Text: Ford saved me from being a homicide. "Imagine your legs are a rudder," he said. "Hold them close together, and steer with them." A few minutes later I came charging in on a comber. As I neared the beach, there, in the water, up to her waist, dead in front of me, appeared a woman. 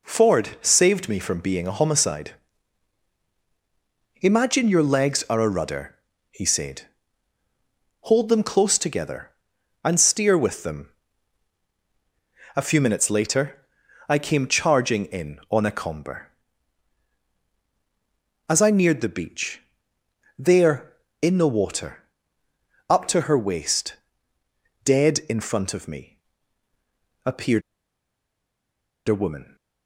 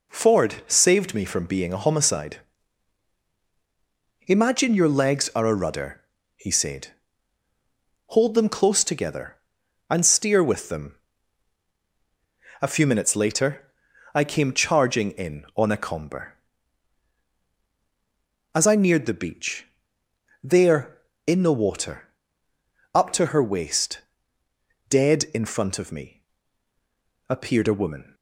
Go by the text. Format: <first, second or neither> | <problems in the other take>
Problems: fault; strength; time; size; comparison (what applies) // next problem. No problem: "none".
second | pauses between "later" and "I"; at 13.6 s; 0.40 s long; also in the second // pauses between "appeared" and "a"; strong; at 27.6 s; 1.4 s long